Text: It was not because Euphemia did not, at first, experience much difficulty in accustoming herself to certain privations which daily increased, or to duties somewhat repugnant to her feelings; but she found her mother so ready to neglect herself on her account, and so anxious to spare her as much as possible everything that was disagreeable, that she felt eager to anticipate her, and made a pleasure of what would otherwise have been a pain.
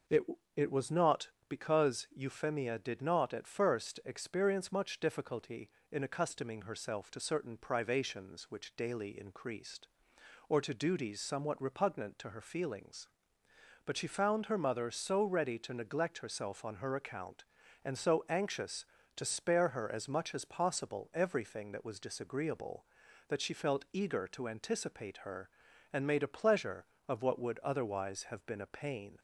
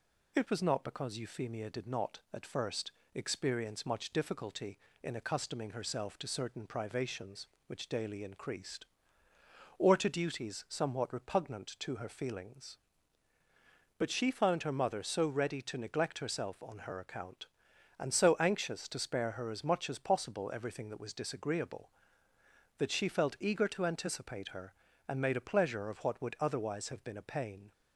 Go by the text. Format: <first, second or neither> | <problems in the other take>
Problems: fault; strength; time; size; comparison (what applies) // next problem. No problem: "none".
second | says "It" twice; at 0.5 s